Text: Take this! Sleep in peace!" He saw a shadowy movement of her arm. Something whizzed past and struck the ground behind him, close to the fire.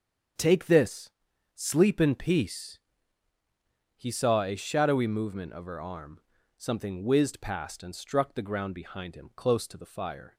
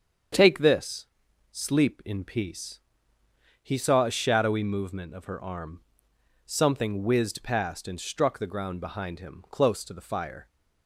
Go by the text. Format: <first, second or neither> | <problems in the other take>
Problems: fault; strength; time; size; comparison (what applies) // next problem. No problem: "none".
neither | starts louder than the rest; strong; the same in both